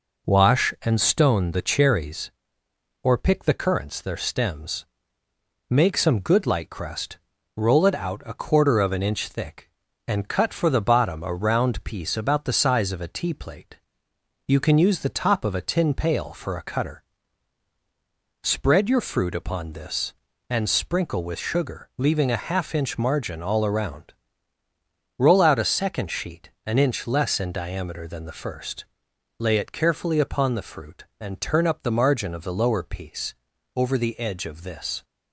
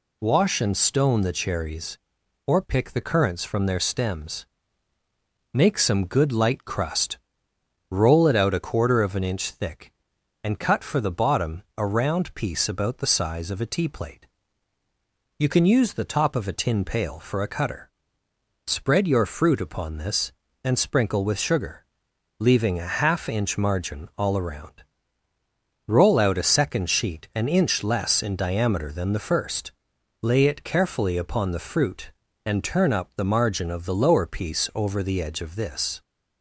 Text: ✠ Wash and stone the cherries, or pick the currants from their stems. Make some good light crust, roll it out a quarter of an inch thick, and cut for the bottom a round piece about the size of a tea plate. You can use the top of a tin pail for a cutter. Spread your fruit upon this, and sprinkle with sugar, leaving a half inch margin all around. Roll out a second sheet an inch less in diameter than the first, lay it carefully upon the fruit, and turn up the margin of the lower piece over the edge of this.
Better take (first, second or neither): second